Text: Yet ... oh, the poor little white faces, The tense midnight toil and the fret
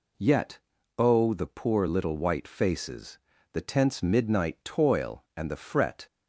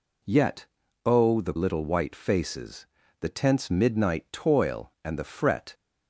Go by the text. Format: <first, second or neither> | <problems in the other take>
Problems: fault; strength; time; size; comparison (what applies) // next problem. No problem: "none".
first | skips "poor"; at 1.5 s